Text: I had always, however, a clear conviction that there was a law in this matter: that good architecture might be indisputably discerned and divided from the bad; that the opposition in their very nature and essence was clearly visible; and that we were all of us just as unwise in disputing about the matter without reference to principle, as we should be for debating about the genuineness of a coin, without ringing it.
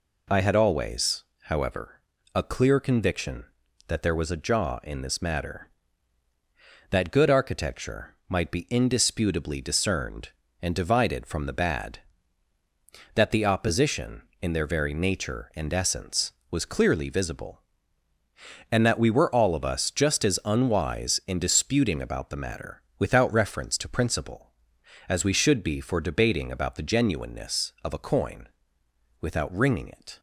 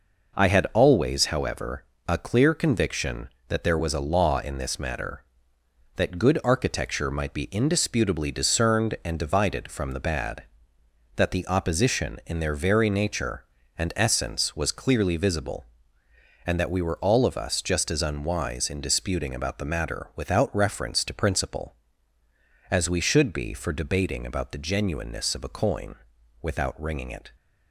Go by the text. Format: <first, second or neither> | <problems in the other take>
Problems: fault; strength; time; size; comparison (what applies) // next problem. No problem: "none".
second | says "jaw" for "law"; at 4.3 s // pauses between "matter" and "without"; slight; at 22.8 s; 0.18 s long